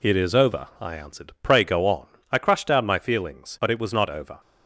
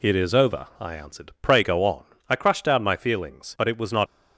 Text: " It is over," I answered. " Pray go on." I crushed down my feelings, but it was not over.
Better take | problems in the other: first | stops before "over"; at 4.0 s

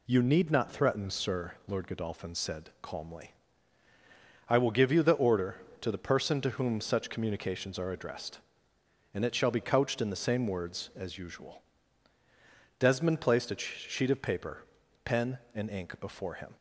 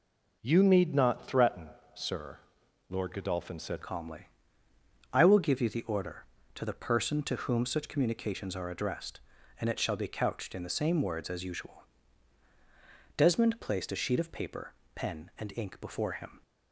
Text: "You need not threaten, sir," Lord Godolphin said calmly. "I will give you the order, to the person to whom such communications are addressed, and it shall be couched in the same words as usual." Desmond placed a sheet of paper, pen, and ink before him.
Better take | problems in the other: first | changes voice at "calmly"; from 3.8 s on; 12.6 s long

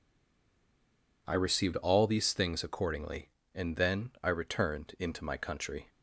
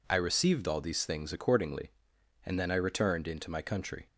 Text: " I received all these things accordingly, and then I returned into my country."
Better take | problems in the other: second | stays silent before the first word; noticeable; until 1.2 s; 1.2 s long

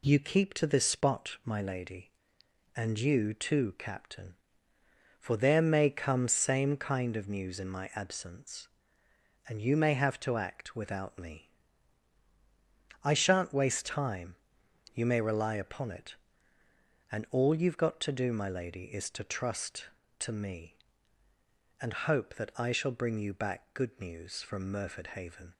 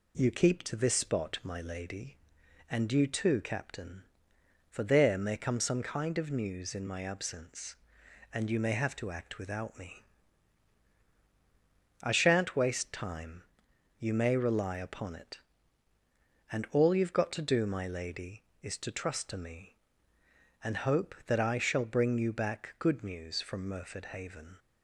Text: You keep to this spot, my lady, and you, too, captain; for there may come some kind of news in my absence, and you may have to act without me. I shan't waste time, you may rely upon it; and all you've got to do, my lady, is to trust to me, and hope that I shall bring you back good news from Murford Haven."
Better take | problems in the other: second | says "same" for "some"; at 6.2 s

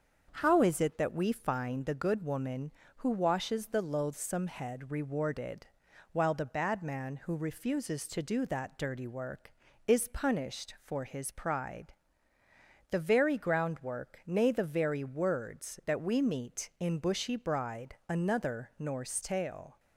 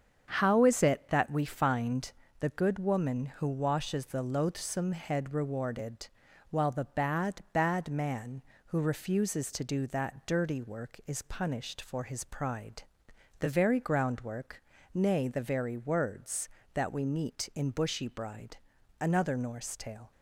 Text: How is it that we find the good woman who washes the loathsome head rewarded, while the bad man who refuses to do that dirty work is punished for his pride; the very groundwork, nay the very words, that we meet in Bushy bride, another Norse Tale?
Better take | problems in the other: first | starts louder than the rest; strong; until 1.3 s; 7 dB; also in the first // pauses between "find" and "the"; slight; at 2.1 s; 0.26 s long // says "bad" twice; at 7.5 s

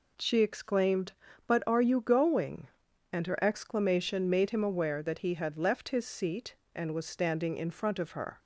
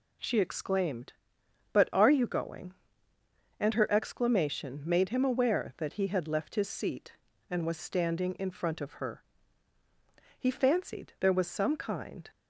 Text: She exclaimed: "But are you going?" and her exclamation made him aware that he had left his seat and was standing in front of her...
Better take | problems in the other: first | goes on to say "He fancied there was some kind"; strong; from 10.3 s on; 1.9 s long

